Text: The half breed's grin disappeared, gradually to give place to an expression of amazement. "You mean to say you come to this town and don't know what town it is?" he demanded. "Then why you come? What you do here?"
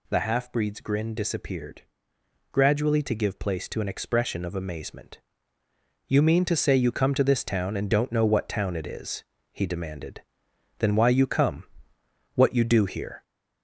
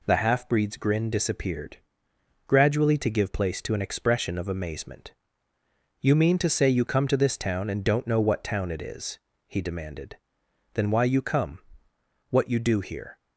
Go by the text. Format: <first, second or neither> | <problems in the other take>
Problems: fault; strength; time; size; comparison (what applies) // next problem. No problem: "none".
second | gets louder; throughout; 3.5 dB